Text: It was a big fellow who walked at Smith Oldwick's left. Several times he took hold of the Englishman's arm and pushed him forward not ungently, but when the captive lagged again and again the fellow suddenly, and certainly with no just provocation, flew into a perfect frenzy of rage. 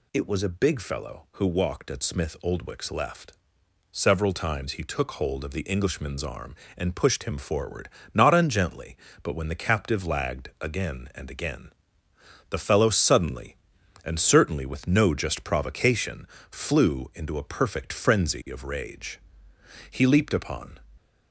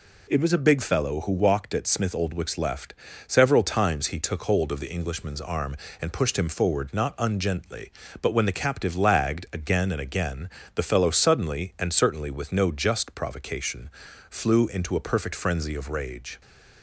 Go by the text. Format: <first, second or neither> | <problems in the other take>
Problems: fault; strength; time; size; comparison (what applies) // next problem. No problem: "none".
second | pauses between "forward" and "not"; slight; at 7.8 s; 0.22 s long // pauses between "again" and "the"; noticeable; at 11.6 s; 0.82 s long; slight in the second // goes on to say "He leaped upon"; noticeable; from 19.8 s on; 0.88 s long